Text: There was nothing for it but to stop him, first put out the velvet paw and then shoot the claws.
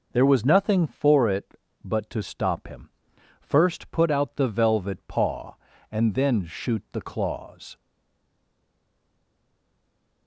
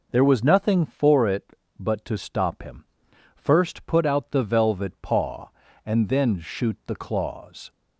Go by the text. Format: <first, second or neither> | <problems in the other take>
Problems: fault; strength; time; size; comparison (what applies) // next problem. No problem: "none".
second | stays silent after the last word; from 7.7 s on; 2.5 s long